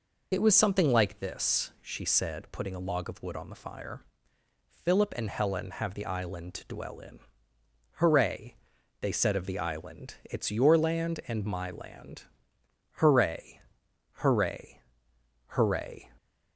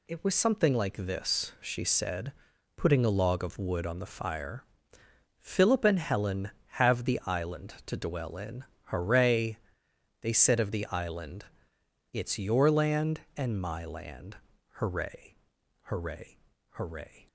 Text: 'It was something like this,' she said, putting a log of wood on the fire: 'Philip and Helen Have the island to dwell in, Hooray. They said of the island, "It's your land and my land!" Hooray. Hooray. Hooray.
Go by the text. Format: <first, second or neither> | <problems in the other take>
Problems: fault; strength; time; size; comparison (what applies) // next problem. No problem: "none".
second | loses the start of "It"; at 0.3 s; 55 ms